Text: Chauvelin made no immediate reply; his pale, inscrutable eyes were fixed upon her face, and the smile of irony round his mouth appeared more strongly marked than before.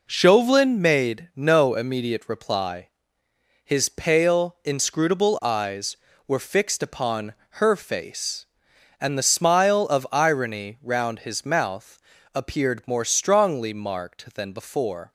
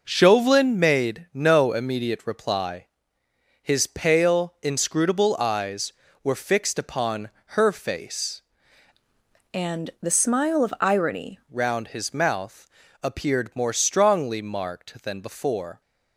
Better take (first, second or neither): first